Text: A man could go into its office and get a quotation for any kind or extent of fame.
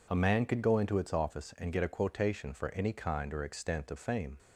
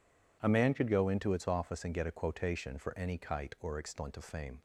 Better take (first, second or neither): first